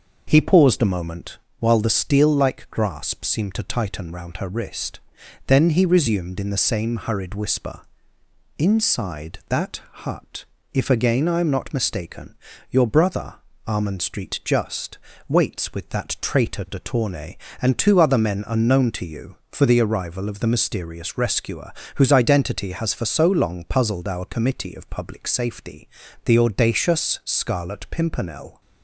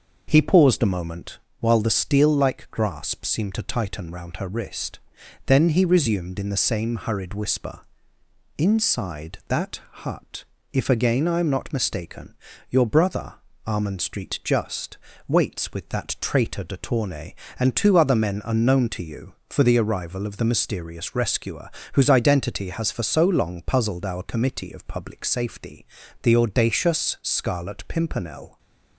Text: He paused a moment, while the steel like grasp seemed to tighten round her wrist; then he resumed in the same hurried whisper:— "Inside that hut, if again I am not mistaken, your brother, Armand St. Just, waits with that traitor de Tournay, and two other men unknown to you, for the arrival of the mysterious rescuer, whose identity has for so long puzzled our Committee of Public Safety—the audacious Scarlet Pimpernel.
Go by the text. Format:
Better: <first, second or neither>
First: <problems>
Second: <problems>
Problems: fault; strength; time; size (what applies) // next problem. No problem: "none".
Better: neither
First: pauses between "that" and "hut"; slight; at 9.8 s; 0.24 s long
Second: pauses between "that" and "hut"; slight; at 9.7 s; 0.24 s long